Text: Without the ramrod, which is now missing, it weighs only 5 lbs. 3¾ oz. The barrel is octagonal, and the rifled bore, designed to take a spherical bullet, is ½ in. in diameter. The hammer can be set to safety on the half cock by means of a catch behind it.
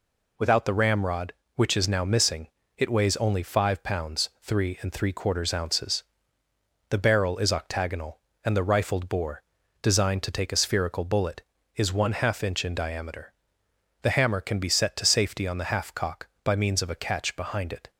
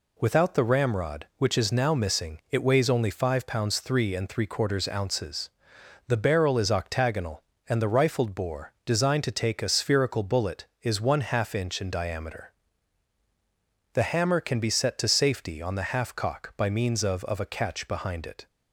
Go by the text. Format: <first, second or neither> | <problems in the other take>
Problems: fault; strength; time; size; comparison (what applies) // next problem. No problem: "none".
first | says "of" twice; at 17.2 s